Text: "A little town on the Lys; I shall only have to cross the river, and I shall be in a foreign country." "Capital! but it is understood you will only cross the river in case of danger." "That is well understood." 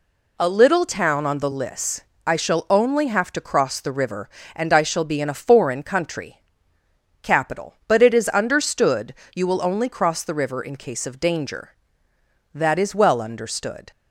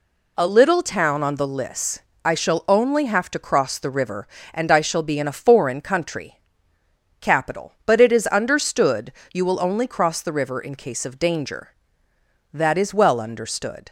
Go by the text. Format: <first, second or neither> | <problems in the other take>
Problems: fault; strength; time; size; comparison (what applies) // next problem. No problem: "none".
neither | pauses between "understood" and "you"; slight; the same in both